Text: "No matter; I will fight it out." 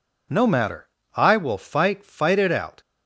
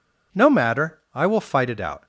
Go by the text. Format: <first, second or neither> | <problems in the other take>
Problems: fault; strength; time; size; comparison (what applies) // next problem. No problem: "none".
second | says "fight" twice; at 2.0 s